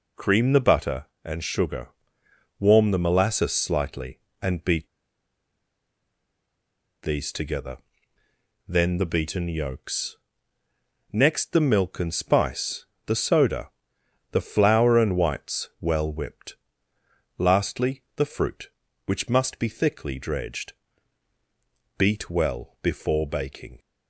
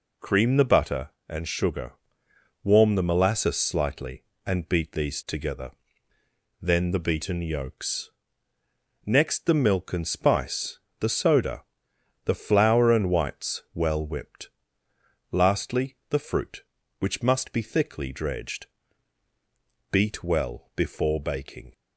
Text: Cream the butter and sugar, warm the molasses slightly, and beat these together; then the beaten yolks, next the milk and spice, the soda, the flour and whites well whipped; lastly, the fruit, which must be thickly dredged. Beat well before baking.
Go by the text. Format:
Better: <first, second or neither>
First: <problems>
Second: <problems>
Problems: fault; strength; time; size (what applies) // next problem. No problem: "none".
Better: second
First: pauses between "beat" and "these"; strong; at 4.8 s; 2.1 s long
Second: none